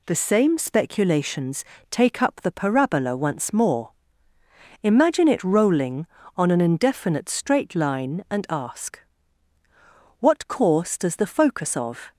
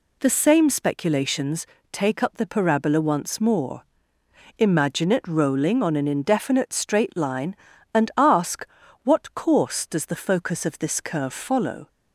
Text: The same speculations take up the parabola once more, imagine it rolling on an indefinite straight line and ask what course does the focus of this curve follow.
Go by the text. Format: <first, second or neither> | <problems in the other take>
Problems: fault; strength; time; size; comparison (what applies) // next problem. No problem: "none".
second | pauses between "speculations" and "take"; slight; at 1.6 s; 0.26 s long; slight in the second // pauses between "ask" and "what"; at 8.9 s; 1.2 s long; also in the second // stops before "this curve follow"; at 12.1 s